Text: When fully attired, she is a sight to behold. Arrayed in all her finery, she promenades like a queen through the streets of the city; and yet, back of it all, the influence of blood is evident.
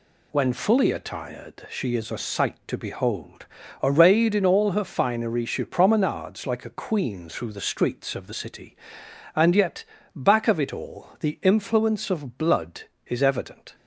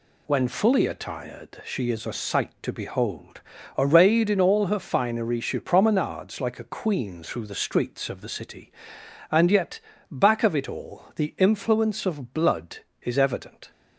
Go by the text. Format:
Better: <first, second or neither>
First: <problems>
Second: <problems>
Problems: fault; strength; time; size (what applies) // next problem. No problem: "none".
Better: neither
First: none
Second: none